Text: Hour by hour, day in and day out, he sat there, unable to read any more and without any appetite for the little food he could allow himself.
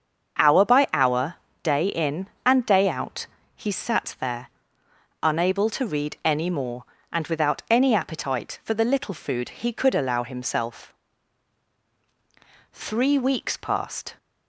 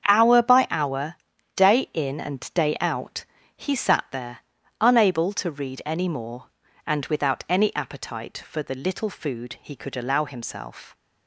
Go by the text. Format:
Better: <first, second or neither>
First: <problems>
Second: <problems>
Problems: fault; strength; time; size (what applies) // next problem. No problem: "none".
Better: second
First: starts louder than the rest; until 1.7 s; 7 dB // goes on to say "Three weeks passed"; from 12.7 s on; 1.4 s long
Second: starts louder than the rest; strong; until 1.0 s; 8 dB